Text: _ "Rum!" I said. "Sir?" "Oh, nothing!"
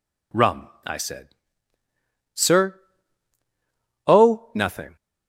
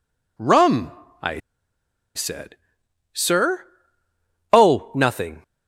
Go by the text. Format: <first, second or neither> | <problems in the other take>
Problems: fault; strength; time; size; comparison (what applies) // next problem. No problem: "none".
first | pauses between "I" and "said"; noticeable; at 1.3 s; 0.75 s long